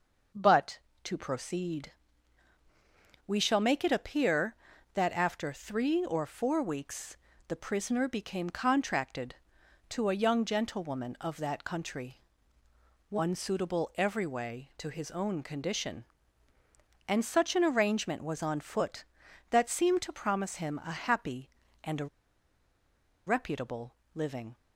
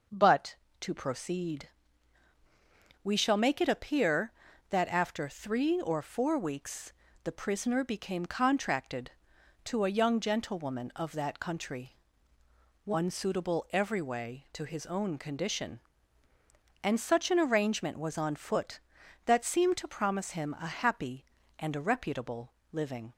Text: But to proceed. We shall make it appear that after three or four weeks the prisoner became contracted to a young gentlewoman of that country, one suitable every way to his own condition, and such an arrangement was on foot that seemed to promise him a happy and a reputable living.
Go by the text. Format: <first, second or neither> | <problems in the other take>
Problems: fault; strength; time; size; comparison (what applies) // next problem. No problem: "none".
second | pauses between "weeks" and "the"; slight; at 7.1 s; 0.30 s long; slight in the second // pauses between "a" and "reputable"; at 22.0 s; 1.1 s long // pauses between "reputable" and "living"; slight; at 23.9 s; 0.22 s long; slight in the second